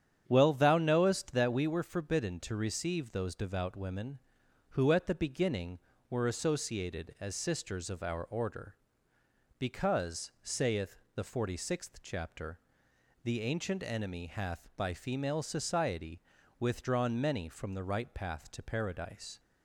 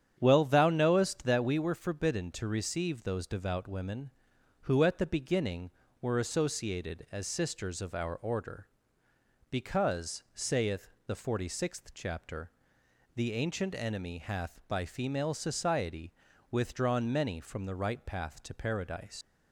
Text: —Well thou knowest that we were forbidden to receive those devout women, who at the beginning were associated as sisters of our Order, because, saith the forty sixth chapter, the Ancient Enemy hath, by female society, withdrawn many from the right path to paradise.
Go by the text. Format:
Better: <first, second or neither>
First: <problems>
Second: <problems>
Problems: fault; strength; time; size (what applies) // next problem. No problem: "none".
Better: first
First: starts louder than the rest; strong; until 1.2 s; 9 dB // pauses between "saith" and "the"; slight; at 10.9 s; 0.18 s long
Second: starts louder than the rest; strong; until 1.1 s; 9 dB // pauses between "saith" and "the"; slight; at 10.8 s; 0.18 s long // leaves "paradise" unfinished; at 19.2 s; 95 ms